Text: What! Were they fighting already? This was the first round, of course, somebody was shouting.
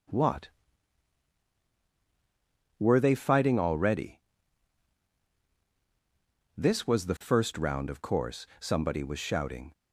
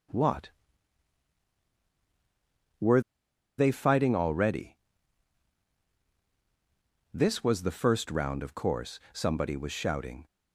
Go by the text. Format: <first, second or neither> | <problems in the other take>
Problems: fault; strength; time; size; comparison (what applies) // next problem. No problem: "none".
first | pauses between "Were" and "they"; noticeable; at 3.0 s; 0.56 s long